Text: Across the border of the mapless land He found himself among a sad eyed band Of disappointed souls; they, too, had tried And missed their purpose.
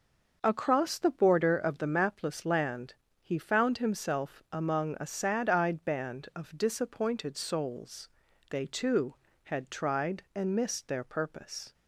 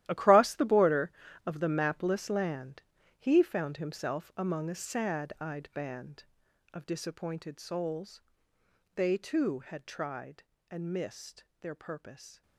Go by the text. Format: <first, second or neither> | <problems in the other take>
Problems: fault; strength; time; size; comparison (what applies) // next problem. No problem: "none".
first | gets quieter; strong; throughout; 14.5 dB // starts louder than the rest; strong; until 1.0 s; 13.5 dB; noticeable in the first // pauses between "land" and "He"; at 2.8 s; 0.38 s long; slight in the first // pauses between "missed" and "their"; slight; at 11.4 s; 0.16 s long